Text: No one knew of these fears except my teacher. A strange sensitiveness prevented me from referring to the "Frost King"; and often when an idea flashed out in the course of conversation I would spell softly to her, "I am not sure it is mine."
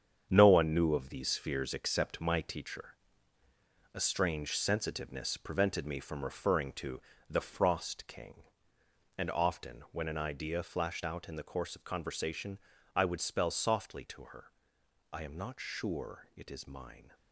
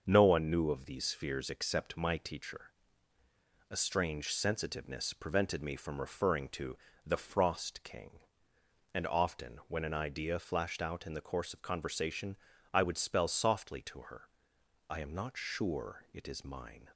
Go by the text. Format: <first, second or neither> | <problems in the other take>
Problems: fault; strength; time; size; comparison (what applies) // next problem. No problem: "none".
second | gets quieter; strong; throughout; 8 dB // starts louder than the rest; strong; until 1.3 s; 8 dB; also in the second // pauses between "to" and "the"; slight; at 7.0 s; 0.30 s long; slight in the second // pauses between "conversation" and "I"; slight; at 12.5 s; 0.34 s long; slight in the second